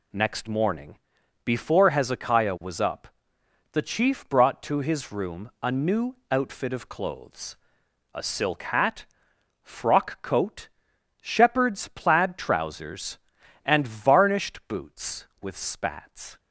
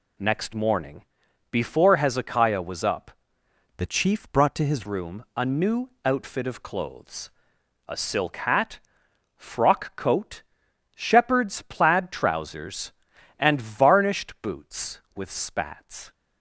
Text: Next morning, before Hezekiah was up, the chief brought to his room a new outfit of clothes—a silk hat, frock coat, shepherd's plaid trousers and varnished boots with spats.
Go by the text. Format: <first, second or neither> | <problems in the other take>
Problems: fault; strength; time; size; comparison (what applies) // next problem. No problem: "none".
first | changes voice from "the" to "his"; from 3.7 to 4.8 s; 1.1 s long